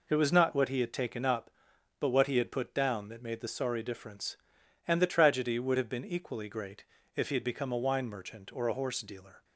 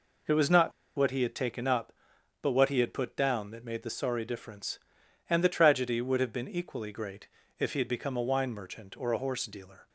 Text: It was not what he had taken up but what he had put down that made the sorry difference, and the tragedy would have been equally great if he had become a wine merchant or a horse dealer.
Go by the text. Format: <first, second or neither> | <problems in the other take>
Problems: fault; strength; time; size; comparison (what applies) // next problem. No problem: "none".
first | pauses between "not" and "what"; slight; at 0.7 s; 0.24 s long // pauses between "great" and "if"; slight; at 7.2 s; 0.32 s long; slight in the first